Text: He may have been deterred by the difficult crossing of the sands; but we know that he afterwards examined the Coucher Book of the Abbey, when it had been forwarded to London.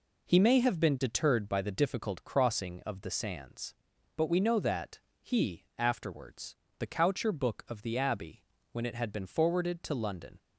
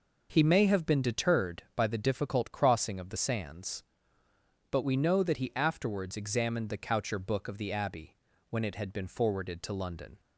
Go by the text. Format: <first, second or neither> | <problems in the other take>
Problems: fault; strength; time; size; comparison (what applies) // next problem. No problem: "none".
second | pauses between "that" and "he"; slight; at 4.9 s; 0.22 s long // skips "examined"; at 6.6 s